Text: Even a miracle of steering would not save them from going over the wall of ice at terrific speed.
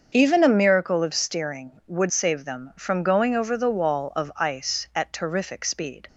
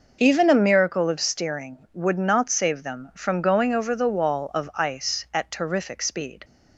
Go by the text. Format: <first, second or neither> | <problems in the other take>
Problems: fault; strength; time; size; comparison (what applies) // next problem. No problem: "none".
second | starts louder than the rest; until 1.1 s; 6.5 dB // skips "not"; at 2.1 s